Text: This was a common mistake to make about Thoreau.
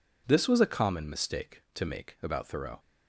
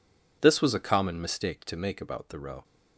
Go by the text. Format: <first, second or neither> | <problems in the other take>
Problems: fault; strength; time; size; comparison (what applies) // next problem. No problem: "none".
neither | none